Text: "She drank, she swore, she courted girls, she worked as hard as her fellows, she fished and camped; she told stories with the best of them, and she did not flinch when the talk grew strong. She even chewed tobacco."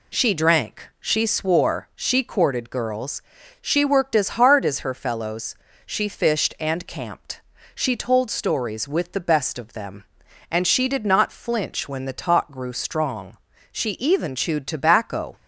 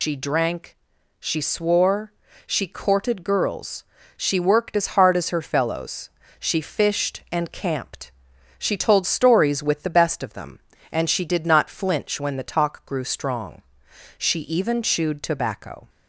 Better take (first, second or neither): first